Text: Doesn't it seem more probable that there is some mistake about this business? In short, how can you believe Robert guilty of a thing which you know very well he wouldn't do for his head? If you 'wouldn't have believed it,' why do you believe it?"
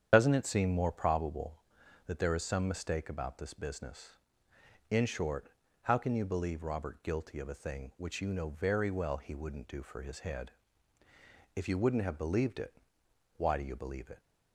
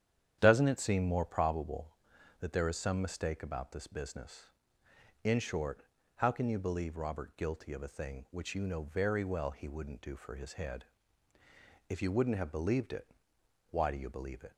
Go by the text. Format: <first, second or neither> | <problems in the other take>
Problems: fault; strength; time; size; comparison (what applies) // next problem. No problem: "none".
second | loses the start of "Doesn't"; at 0.1 s; 70 ms // starts louder than the rest; strong; until 1.1 s; 8.5 dB; strong in the second